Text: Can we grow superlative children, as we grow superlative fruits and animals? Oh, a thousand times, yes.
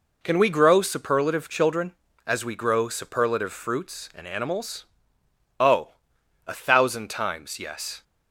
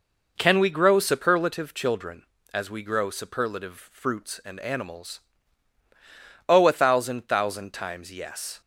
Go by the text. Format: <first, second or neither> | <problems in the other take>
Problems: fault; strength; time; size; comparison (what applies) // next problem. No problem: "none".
first | says "thousand" twice; at 7.2 s